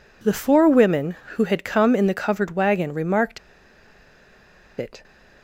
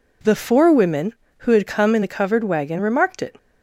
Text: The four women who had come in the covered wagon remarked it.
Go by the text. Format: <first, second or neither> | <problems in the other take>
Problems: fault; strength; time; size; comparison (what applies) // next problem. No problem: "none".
second | pauses between "remarked" and "it"; strong; at 3.3 s; 1.4 s long